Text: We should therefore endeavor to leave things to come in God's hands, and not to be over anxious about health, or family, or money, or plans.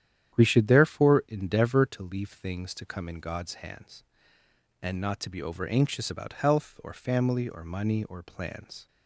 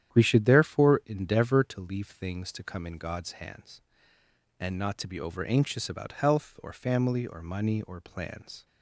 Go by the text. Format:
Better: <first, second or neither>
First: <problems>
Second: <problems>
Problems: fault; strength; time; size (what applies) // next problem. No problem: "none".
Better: neither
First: starts louder than the rest; strong; until 1.3 s; 10 dB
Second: starts louder than the rest; strong; until 1.1 s; 10 dB